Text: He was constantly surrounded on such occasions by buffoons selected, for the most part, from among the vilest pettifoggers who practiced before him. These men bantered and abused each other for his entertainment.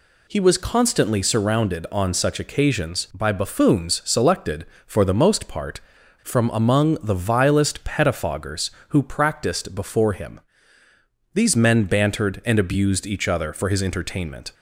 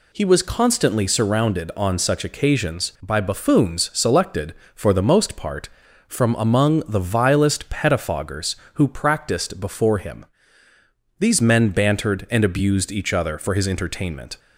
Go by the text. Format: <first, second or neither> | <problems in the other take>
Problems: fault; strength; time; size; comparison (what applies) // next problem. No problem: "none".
neither | none